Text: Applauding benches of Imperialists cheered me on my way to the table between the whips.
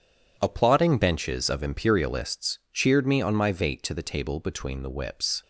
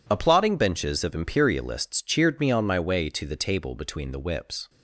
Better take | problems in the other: second | says "vate" for "way"; at 3.5 s

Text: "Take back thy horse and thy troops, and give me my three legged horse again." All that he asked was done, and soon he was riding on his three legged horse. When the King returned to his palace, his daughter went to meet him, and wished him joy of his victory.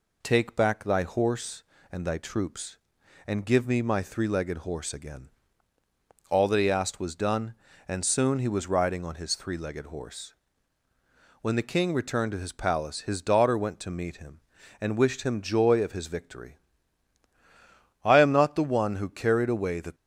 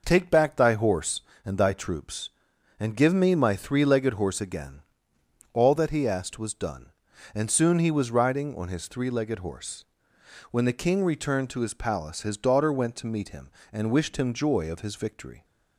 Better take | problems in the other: second | goes on to say "I am not the one who carried away the"; strong; from 18.0 s on; 1.9 s long

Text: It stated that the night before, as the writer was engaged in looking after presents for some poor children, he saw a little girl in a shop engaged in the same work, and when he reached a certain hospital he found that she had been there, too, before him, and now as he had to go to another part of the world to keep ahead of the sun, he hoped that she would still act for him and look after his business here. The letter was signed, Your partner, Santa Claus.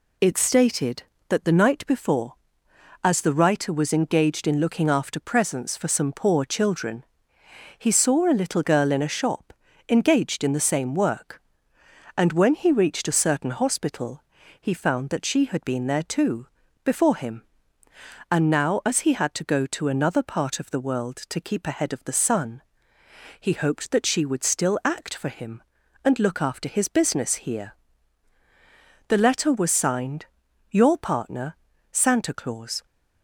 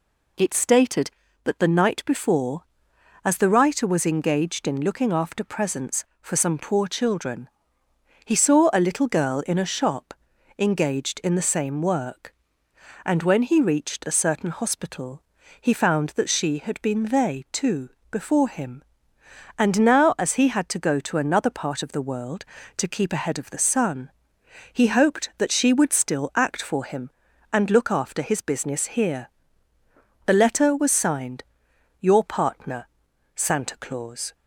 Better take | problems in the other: first | pauses between "shop" and "engaged"; at 10.1 s; 0.44 s long; slight in the first // pauses between "hospital" and "he"; at 15.2 s; 0.38 s long; also in the first // says "they" for "there"; at 17.0 s

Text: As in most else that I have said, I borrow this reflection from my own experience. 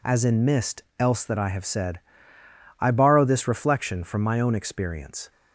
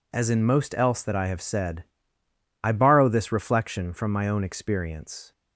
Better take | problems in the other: second | says "mist" for "most"; at 0.4 s

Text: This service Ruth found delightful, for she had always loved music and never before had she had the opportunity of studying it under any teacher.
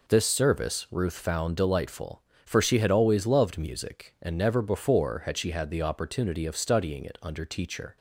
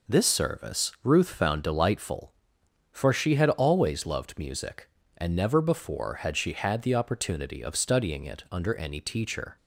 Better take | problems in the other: second | skips "any"; at 7.4 s

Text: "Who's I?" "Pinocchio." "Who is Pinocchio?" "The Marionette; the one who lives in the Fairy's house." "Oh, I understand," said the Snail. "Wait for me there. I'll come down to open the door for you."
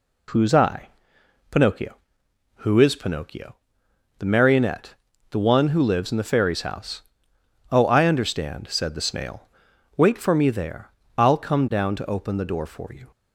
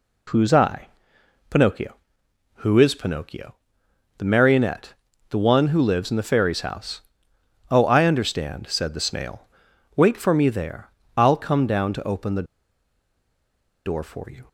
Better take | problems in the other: first | pauses between "the" and "door"; strong; at 12.4 s; 1.3 s long

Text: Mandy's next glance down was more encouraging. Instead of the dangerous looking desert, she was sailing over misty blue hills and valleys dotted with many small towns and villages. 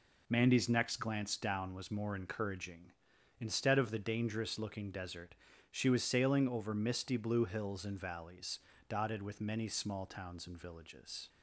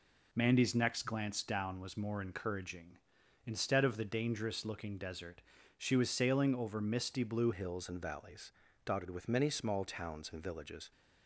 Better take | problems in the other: first | changes voice at "hills"; from 7.5 s on; 3.4 s long // pauses between "valleys" and "dotted"; slight; at 8.5 s; 0.34 s long; slight in the first

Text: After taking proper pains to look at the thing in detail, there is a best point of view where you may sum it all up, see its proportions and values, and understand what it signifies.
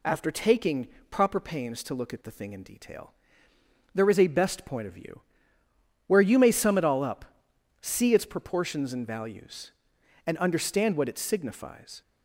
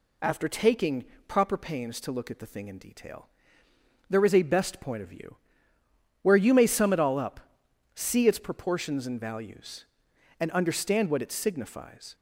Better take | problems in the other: neither | pauses between "taking" and "proper"; slight; the same in both // pauses between "view" and "where"; noticeable; the same in both

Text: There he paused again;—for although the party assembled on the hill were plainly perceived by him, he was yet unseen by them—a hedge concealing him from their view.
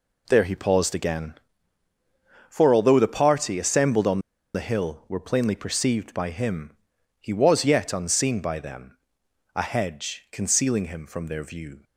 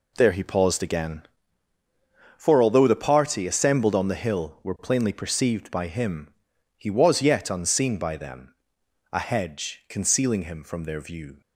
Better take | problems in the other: second | pauses between "on" and "the"; slight; at 4.2 s; 0.34 s long

